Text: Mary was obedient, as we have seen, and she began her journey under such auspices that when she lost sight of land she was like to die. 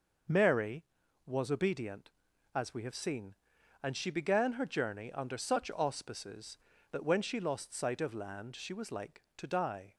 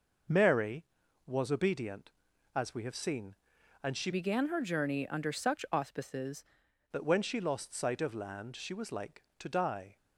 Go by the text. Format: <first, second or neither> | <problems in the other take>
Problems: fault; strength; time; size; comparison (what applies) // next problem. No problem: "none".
first | changes voice from "began" to "auspices"; from 4.1 to 6.4 s; 2.3 s long